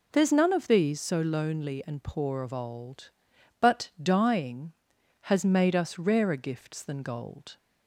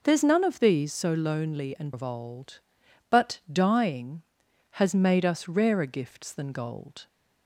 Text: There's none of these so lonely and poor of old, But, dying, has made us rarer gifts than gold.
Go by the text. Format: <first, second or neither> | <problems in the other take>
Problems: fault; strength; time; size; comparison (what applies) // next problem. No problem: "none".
first | skips "poor"; at 1.9 s